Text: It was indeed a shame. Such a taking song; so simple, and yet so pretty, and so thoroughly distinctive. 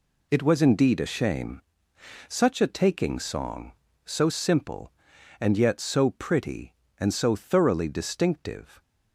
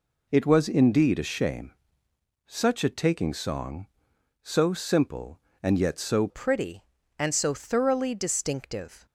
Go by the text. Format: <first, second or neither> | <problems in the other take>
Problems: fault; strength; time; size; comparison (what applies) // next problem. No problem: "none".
first | changes voice at "pretty"; from 6.2 s on; 2.8 s long